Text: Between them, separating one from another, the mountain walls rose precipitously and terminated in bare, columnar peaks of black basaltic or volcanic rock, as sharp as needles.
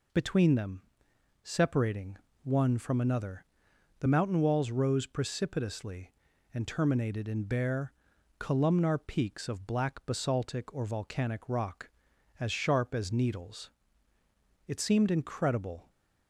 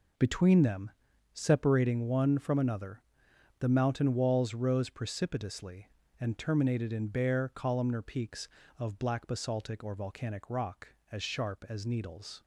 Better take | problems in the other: second | pauses between "separating" and "one"; slight; at 2.1 s; 0.26 s long // goes on to say "It seemed incredible"; noticeable; from 14.6 s on; 1.2 s long

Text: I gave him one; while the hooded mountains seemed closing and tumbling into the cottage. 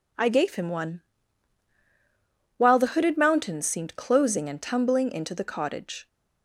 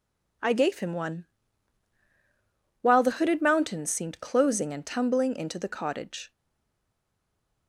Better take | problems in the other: first | stays silent after the last word; noticeable; from 6.3 s on; 1.3 s long

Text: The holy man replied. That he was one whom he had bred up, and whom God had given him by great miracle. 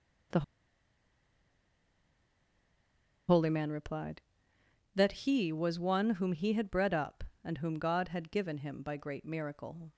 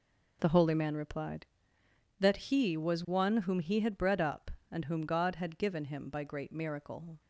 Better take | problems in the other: second | pauses between "The" and "holy"; strong; at 0.4 s; 2.8 s long

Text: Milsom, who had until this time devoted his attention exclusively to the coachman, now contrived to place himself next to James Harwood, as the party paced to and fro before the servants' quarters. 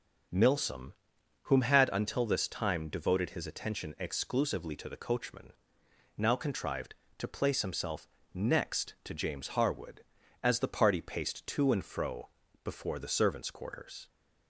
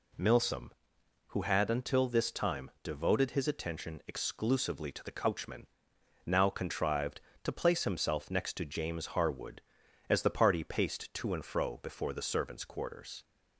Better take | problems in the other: second | starts louder than the rest; noticeable; until 1.8 s; 6 dB // says "whom" for "who"; at 1.4 s // pauses between "himself" and "next"; slight; at 8.0 s; 0.26 s long // pauses between "fro" and "before"; slight; at 12.2 s; 0.36 s long

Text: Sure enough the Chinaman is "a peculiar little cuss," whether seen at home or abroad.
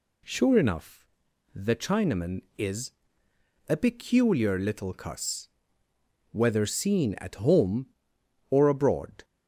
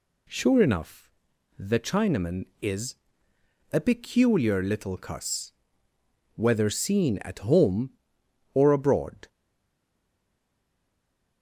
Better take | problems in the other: first | pauses between "enough" and "the"; noticeable; at 1.0 s; 0.50 s long; noticeable in the first // pauses between "is" and "a"; noticeable; at 2.9 s; 0.76 s long; noticeable in the first // stays silent after the last word; from 9.2 s on; 2.2 s long

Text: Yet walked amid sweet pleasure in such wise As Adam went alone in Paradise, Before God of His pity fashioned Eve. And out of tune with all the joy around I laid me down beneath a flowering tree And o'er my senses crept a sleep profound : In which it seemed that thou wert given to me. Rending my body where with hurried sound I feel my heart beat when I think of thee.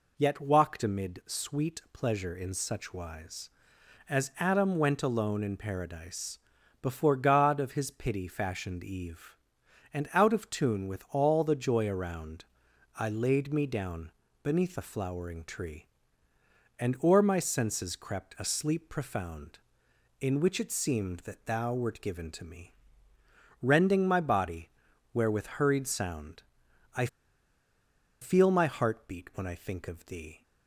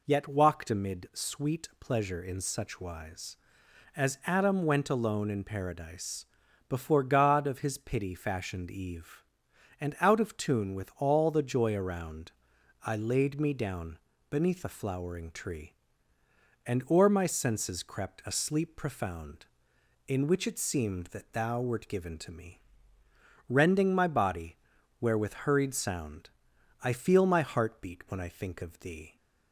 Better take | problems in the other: second | pauses between "around" and "I"; noticeable; at 12.4 s; 0.52 s long; noticeable in the second // pauses between "down" and "beneath"; slight; at 14.1 s; 0.32 s long; slight in the second // pauses between "body" and "where"; at 24.6 s; 0.44 s long; also in the second // pauses between "sound" and "I"; noticeable; at 26.4 s; 0.52 s long; noticeable in the second // pauses between "I" and "feel"; at 27.0 s; 1.1 s long

